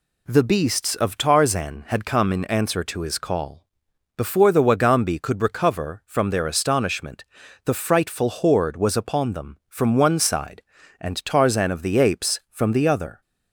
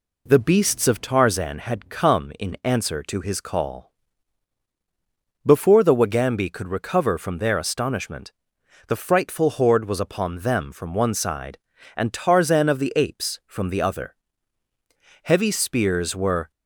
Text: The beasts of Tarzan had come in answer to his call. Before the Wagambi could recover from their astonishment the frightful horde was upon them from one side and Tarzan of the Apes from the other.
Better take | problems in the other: first | pauses between "astonishment" and "the"; noticeable; at 8.3 s; 0.56 s long; also in the first // goes on to say "Heavy spears were"; noticeable; from 15.2 s on; 1.2 s long

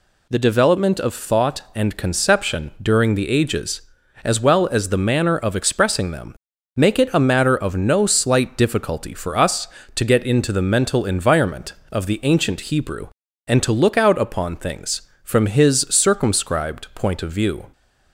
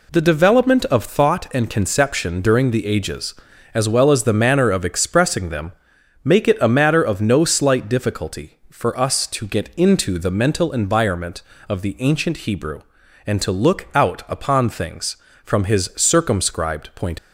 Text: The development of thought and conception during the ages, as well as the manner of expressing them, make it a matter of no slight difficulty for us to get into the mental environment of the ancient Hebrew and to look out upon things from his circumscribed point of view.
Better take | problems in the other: first | stops before "of view"; at 17.1 s

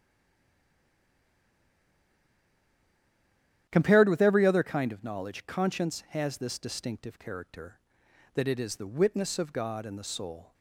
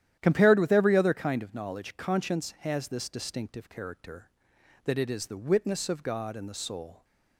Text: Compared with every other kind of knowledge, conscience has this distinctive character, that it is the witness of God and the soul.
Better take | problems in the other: second | stays silent before the first word; strong; until 3.6 s; 3.6 s long // starts louder than the rest; strong; until 4.7 s; 11 dB; strong in the second

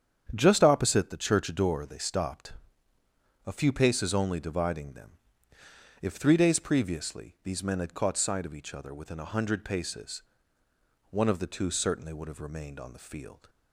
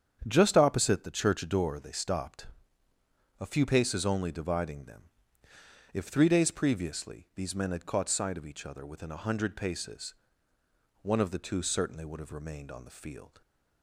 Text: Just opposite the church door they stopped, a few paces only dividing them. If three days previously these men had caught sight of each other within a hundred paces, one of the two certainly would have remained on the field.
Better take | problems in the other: neither | starts louder than the rest; strong; the same in both

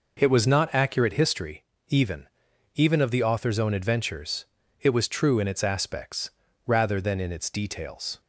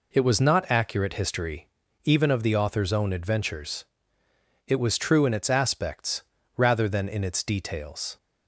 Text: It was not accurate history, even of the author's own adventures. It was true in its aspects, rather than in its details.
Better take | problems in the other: second | says "even" twice; at 2.7 s

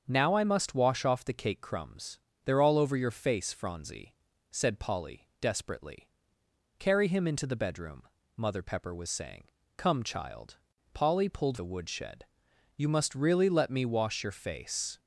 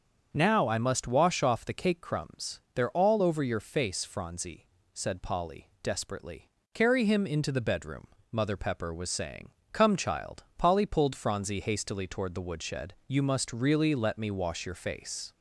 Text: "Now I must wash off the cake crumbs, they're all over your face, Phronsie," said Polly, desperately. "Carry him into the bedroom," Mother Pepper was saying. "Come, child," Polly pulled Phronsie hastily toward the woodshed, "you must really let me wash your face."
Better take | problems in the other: second | starts louder than the rest; until 1.0 s; 7 dB; also in the second // skips "Phronsie hastily toward"; at 11.5 s

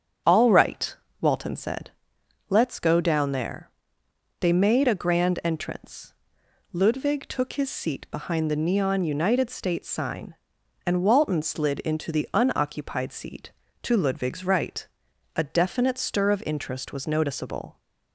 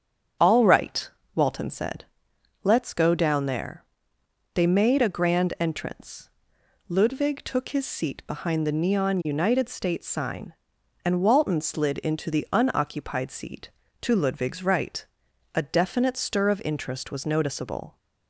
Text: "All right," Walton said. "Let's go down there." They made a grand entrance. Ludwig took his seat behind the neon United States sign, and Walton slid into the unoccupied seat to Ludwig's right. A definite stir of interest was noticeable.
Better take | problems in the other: neither | starts louder than the rest; strong; the same in both

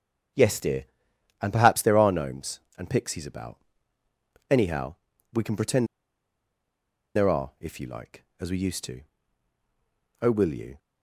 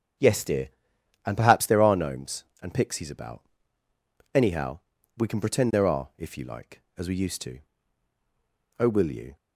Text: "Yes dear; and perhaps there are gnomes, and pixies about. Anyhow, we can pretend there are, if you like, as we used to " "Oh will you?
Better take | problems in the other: second | starts louder than the rest; strong; until 1.9 s; 8.5 dB; strong in the second // pauses between "pretend" and "there"; strong; at 5.8 s; 1.2 s long

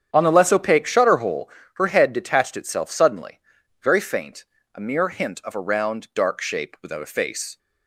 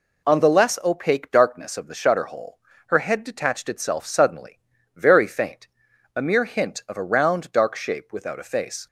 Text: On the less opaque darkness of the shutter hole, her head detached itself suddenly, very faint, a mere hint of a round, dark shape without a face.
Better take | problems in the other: second | starts louder than the rest; strong; until 1.1 s; 8.5 dB // skips "darkness of the"; at 0.8 s

